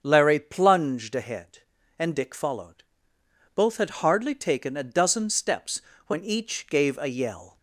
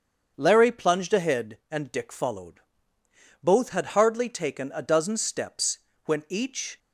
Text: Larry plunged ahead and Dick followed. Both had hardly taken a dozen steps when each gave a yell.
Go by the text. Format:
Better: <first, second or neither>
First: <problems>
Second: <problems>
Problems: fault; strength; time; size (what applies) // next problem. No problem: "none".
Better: first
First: starts louder than the rest; strong; until 1.0 s; 7 dB // pauses between "steps" and "when"; slight; at 5.8 s; 0.26 s long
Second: starts louder than the rest; until 1.3 s; 7 dB // pauses between "steps" and "when"; slight; at 5.7 s; 0.28 s long // stops before "gave a yell"; at 6.7 s